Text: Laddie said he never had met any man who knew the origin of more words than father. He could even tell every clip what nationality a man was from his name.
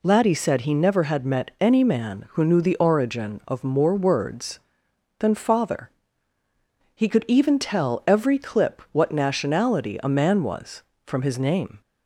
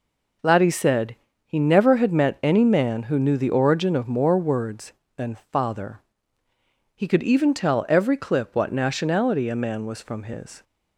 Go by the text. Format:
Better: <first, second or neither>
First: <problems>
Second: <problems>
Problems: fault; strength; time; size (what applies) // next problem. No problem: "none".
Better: first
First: none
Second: pauses between "said" and "he"; slight; at 1.1 s; 0.30 s long // stops before "name"; at 10.6 s